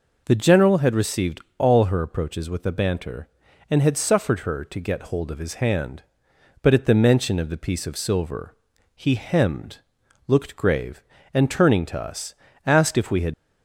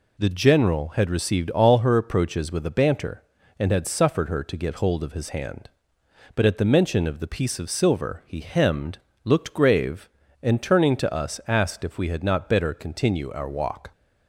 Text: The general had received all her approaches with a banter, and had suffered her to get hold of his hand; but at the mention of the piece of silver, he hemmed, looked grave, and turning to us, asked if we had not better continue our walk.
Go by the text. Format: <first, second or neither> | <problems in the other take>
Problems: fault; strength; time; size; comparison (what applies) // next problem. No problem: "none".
second | pauses between "received" and "all"; slight; at 1.3 s; 0.18 s long // stops before "not better continue our walk"; at 13.3 s